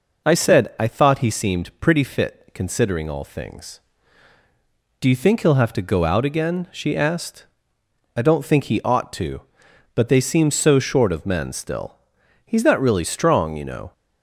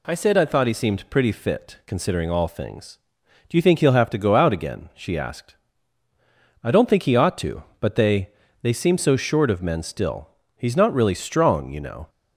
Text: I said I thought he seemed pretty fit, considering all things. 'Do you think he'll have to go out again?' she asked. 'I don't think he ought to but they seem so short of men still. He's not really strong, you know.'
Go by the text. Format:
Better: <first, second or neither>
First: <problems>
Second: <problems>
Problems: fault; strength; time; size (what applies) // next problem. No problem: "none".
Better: first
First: none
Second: says "they" twice; at 8.6 s